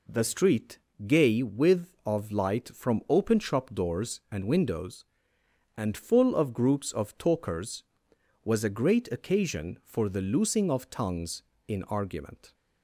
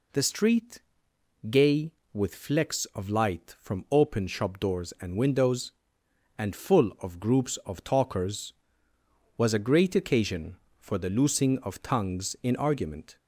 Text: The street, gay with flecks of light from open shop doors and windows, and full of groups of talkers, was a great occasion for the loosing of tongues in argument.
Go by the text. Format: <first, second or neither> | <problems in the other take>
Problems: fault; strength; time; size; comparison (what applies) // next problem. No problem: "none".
second | skips "flecks"; at 1.9 s